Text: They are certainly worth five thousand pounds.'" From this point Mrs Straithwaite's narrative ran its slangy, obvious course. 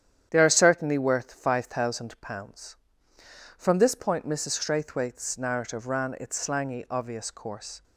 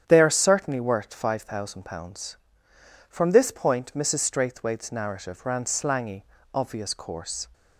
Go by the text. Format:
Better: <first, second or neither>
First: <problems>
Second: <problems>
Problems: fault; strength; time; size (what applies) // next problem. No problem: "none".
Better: first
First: starts louder than the rest; strong; until 1.3 s; 10 dB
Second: starts louder than the rest; strong; until 1.0 s; 9 dB // skips "its"; at 5.6 s